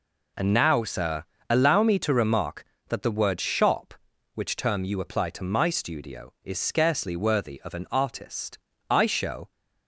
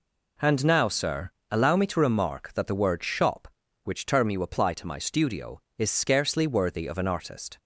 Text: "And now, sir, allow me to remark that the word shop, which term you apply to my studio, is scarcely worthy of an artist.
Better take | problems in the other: second | goes on to say "I show"; noticeable; from 8.8 s on; 0.62 s long

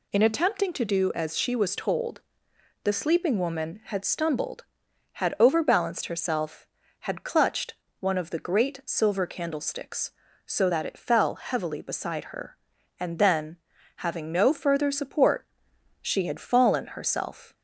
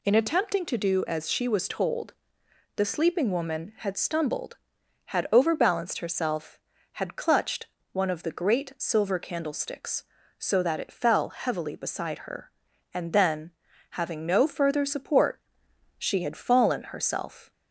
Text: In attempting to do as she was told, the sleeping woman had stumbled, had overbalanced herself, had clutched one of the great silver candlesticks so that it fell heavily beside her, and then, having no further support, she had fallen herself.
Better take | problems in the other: neither | pauses between "clutched" and "one"; slight; the same in both

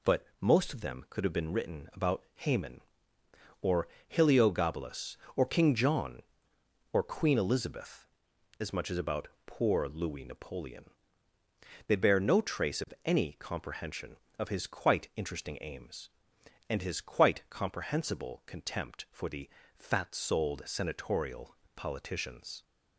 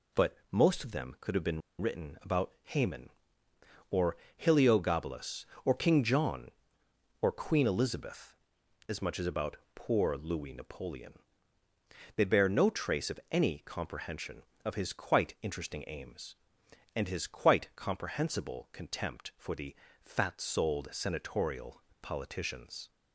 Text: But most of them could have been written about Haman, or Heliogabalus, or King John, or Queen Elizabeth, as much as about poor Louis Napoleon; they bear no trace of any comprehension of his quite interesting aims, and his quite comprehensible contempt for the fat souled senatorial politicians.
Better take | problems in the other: first | pauses between "But" and "most"; slight; at 0.3 s; 0.16 s long; slight in the first // pauses between "been" and "written"; slight; at 1.6 s; 0.19 s long // pauses between "or" and "Heliogabalus"; slight; at 4.1 s; 0.20 s long; slight in the first // pauses between "about" and "poor"; slight; at 9.5 s; 0.18 s long; slight in the first // pauses between "the" and "fat"; slight; at 19.7 s; 0.30 s long; slight in the first // pauses between "senatorial" and "politicians"; slight; at 21.8 s; 0.20 s long; slight in the first

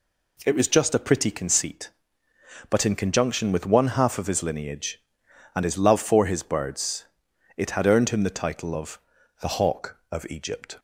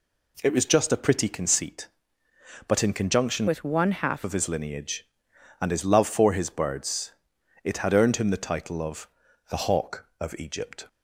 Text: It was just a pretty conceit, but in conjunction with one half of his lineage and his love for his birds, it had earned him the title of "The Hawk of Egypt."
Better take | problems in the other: first | changes voice from "with" to "half"; from 3.4 to 4.2 s; 0.8 s long // pauses between "of" and "The"; at 9.0 s; 0.42 s long; also in the first

